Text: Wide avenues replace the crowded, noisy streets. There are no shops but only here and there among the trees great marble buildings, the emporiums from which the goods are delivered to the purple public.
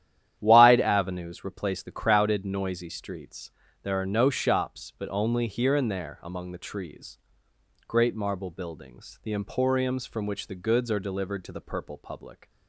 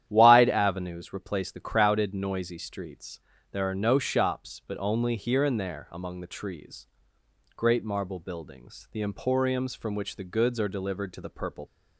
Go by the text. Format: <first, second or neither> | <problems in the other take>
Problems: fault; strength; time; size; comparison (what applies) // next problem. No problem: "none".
first | starts louder than the rest; strong; until 1.0 s; 11 dB; strong in the first // pauses between "trees" and "great"; noticeable; at 6.8 s; 0.70 s long; noticeable in the first // stops before "public"; at 11.6 s